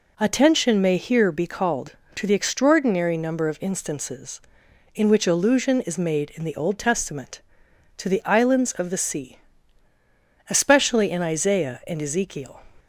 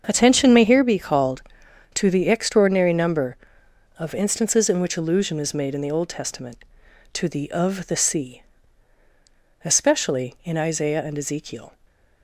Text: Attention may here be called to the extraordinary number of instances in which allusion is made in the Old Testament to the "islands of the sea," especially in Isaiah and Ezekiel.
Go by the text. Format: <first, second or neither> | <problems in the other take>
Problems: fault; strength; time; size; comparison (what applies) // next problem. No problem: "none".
first | starts louder than the rest; until 1.0 s; 6.5 dB // skips "islands"; at 7.5 s